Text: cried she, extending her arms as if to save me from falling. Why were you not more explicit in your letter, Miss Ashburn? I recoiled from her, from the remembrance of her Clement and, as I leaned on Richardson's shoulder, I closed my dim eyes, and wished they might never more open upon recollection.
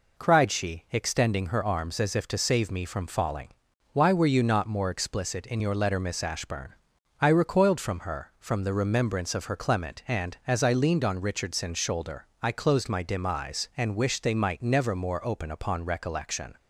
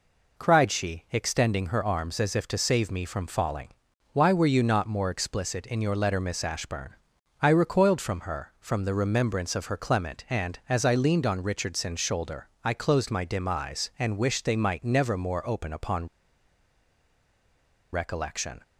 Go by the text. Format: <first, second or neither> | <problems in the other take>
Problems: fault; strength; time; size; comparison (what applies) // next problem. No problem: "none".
first | pauses between "upon" and "recollection"; strong; at 16.0 s; 1.8 s long